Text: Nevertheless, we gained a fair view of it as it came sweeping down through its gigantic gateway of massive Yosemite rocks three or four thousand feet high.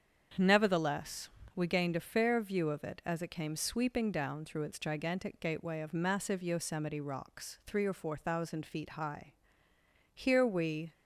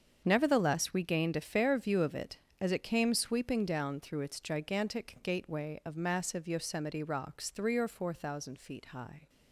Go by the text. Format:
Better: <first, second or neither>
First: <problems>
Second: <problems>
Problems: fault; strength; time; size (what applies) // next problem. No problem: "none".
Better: second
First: starts louder than the rest; strong; until 1.6 s; 7.5 dB // goes on to say "Here we"; noticeable; from 10.1 s on; 0.78 s long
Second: starts louder than the rest; strong; until 1.2 s; 7 dB